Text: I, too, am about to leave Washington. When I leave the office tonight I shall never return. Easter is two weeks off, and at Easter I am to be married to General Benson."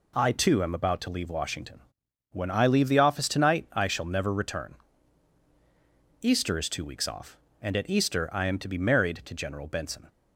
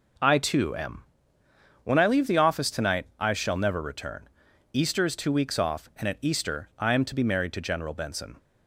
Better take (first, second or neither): first